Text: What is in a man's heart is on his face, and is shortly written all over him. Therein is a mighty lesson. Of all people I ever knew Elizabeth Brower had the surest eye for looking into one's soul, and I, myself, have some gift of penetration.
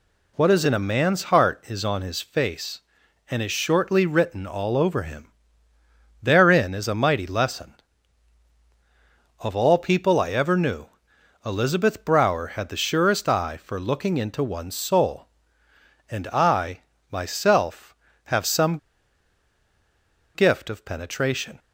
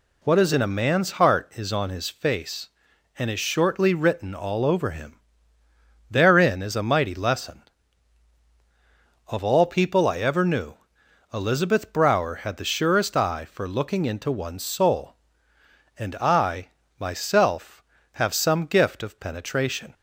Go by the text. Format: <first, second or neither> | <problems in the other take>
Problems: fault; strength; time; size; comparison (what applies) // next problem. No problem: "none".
second | pauses between "knew" and "Elizabeth"; noticeable; at 10.8 s; 0.60 s long; noticeable in the second // pauses between "some" and "gift"; strong; at 18.7 s; 1.5 s long